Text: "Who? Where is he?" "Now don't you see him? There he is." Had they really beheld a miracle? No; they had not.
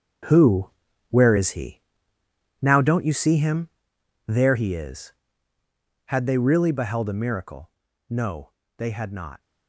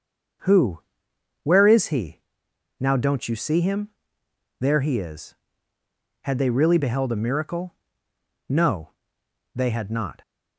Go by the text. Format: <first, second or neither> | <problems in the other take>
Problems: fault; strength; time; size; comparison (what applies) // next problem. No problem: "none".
second | gets quieter; strong; throughout; 10.5 dB // starts louder than the rest; strong; until 1.6 s; 7 dB; also in the second